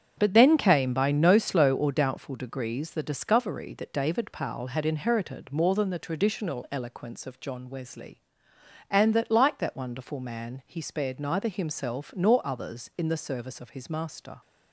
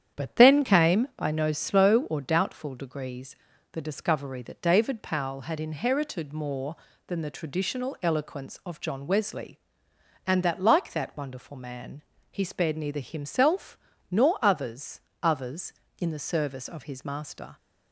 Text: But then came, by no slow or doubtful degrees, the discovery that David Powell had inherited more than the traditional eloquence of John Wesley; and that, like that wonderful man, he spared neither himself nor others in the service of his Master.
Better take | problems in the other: first | starts louder than the rest; strong; until 1.2 s; 9 dB; strong in the first // pauses between "himself" and "nor"; slight; at 13.7 s; 0.36 s long // says "others" twice; at 15.2 s

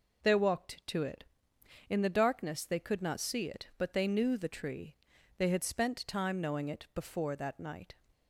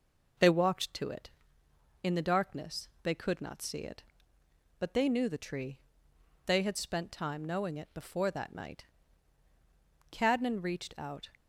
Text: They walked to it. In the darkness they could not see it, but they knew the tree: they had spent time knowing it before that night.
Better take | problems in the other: first | pauses between "darkness" and "they"; slight; at 2.8 s; 0.16 s long // goes on to say "Cadnan reached out"; noticeable; from 10.1 s on; 1.1 s long

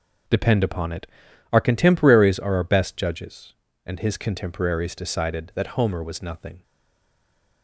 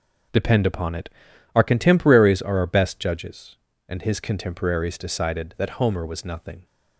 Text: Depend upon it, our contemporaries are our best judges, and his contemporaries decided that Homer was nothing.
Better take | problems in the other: second | stays silent after the last word; from 6.6 s on; 1.0 s long

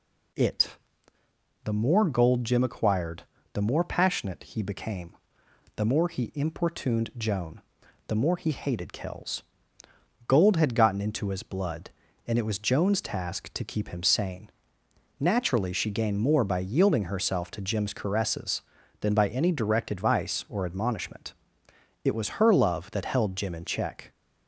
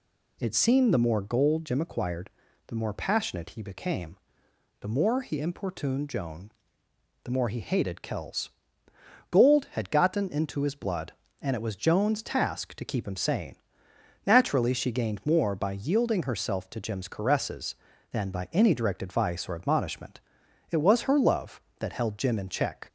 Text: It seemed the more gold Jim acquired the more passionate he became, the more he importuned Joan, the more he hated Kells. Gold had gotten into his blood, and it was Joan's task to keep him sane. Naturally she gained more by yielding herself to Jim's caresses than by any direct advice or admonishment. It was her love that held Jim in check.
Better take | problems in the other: second | skips "seemed"; at 1.2 s // pauses between "acquired" and "the"; slight; at 3.2 s; 0.30 s long; also in the second

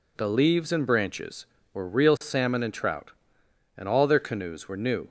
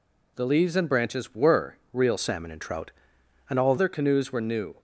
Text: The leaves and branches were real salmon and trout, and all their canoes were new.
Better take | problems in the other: first | pauses between "were" and "real"; slight; at 1.7 s; 0.16 s long // changes voice from "salmon" to "all"; from 2.1 to 3.7 s; 1.6 s long

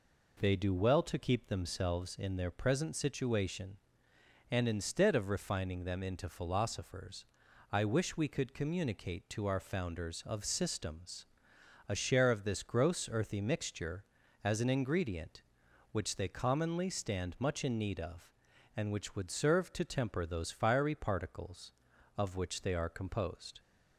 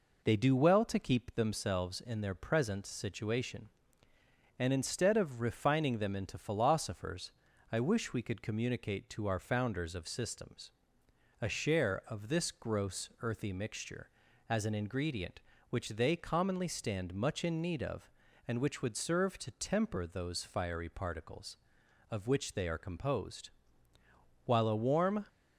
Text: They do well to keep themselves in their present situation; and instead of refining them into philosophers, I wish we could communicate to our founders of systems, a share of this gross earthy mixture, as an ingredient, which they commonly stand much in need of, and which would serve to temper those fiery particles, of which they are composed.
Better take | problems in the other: first | goes on to say "While a warm"; noticeable; from 24.4 s on; 0.80 s long

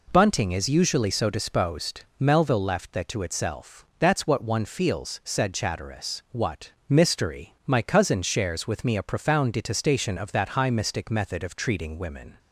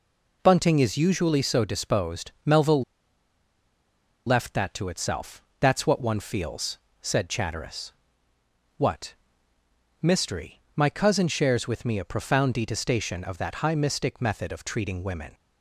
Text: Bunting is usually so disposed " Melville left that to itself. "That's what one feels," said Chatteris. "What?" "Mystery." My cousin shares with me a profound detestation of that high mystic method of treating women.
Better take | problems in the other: first | pauses between "Melville" and "left"; strong; at 2.8 s; 1.4 s long

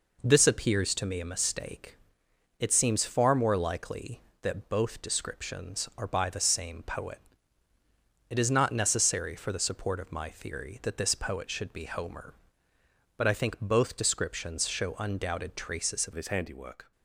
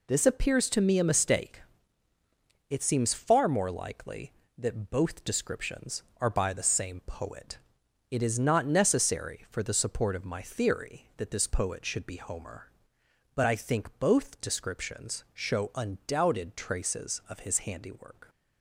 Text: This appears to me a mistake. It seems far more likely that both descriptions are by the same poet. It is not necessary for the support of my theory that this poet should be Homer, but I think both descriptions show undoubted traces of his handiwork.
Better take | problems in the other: second | changes voice at "his"; from 16.1 s on; 0.8 s long

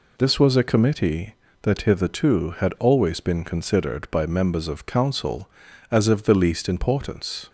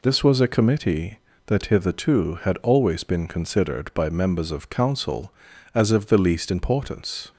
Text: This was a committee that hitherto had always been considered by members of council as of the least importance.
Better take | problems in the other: neither | none

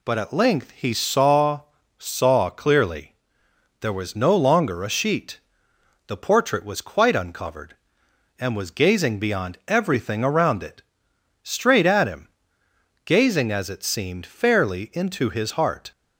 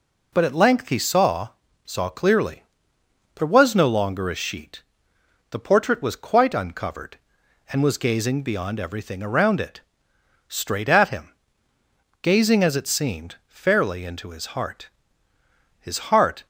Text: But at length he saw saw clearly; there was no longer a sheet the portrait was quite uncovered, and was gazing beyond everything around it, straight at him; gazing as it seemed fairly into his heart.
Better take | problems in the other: first | pauses between "saw" and "saw"; slight; at 1.4 s; 0.36 s long; slight in the first // pauses between "sheet" and "the"; noticeable; at 4.8 s; 0.70 s long; noticeable in the first // goes on to say "His heart"; noticeable; from 15.7 s on; 0.66 s long

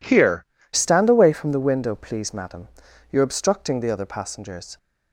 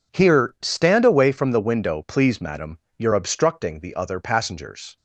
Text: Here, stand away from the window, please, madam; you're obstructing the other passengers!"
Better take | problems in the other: second | changes voice at "stand"; from 0.7 s on; 4.0 s long

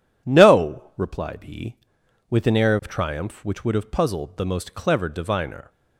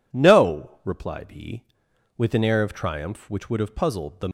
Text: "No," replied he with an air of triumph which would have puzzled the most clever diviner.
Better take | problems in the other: first | stops before "most clever diviner"; at 4.2 s

